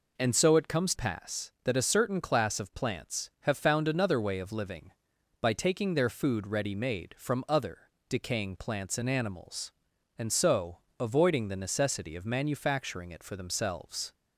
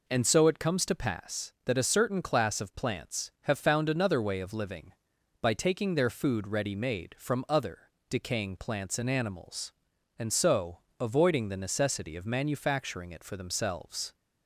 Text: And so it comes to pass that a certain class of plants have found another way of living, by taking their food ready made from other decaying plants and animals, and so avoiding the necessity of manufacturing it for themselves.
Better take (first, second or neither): second